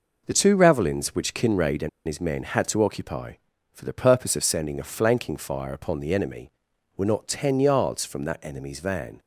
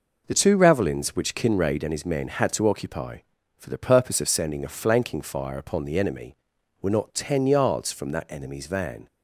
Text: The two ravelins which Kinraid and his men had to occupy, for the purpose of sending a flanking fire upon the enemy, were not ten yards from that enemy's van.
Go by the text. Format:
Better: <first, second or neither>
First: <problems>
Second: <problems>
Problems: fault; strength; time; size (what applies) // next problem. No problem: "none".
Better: second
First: pauses between "and" and "his"; slight; at 1.8 s; 0.17 s long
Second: none